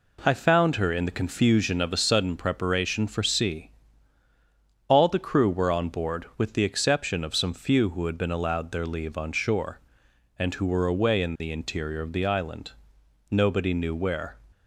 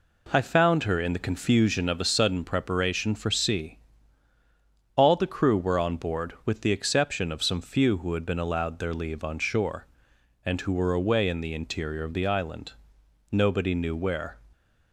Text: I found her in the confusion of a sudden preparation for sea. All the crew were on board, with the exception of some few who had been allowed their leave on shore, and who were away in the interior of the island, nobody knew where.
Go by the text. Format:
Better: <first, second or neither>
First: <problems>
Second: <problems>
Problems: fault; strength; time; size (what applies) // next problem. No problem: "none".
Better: neither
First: none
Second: none